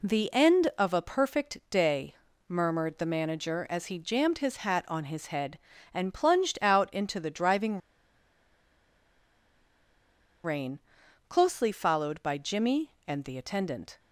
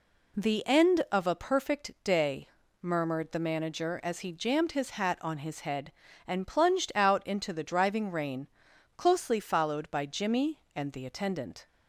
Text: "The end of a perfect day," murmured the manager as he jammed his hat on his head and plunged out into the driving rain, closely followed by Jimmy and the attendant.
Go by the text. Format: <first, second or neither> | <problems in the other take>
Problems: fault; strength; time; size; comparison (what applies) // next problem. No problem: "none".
second | pauses between "driving" and "rain"; strong; at 7.7 s; 2.6 s long